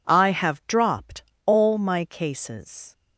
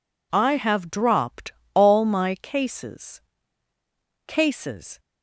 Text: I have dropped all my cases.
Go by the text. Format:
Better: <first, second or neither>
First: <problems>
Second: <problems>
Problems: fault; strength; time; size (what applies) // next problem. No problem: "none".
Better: first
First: pauses between "dropped" and "all"; slight; at 1.2 s; 0.24 s long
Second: pauses between "dropped" and "all"; slight; at 1.5 s; 0.20 s long // says "cases" twice; at 4.2 s